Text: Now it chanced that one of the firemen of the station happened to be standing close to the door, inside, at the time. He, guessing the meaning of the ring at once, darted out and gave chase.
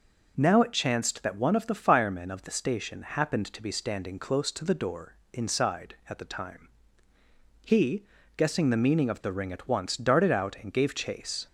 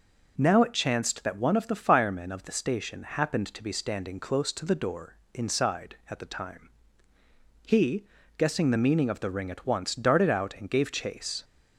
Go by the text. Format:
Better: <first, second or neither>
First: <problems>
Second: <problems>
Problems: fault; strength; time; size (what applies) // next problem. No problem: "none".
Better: neither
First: none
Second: none